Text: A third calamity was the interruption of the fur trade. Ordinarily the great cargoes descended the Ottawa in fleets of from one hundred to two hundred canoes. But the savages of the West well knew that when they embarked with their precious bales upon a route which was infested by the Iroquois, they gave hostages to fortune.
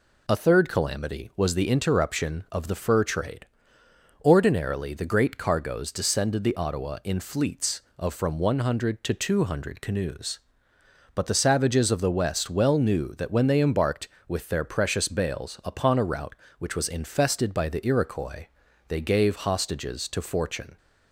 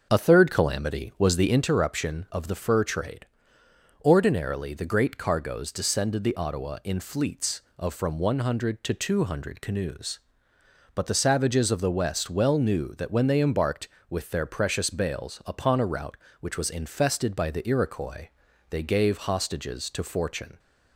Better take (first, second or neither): first